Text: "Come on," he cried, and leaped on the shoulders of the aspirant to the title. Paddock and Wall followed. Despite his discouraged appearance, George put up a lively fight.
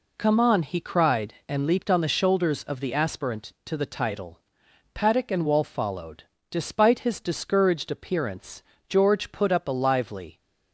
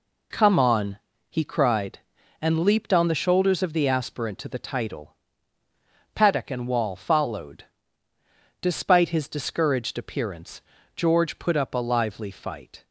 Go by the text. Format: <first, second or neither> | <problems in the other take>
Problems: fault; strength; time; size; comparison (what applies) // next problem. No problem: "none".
second | stops before "fight"; at 10.3 s